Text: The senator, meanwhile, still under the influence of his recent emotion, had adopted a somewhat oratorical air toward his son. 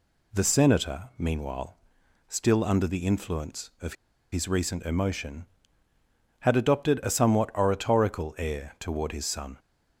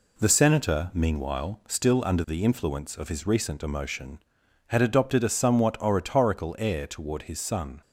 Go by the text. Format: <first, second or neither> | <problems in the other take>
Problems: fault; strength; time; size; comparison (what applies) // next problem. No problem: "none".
second | pauses between "of" and "his"; at 3.9 s; 0.38 s long